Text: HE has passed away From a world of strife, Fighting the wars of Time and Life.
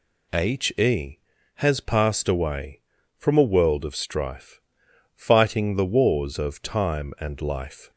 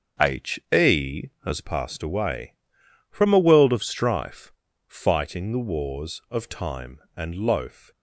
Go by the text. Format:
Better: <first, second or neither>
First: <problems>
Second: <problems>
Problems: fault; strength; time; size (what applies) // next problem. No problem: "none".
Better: first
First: none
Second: starts louder than the rest; until 1.4 s; 6.5 dB // says "Loaf" for "Life"; at 7.3 s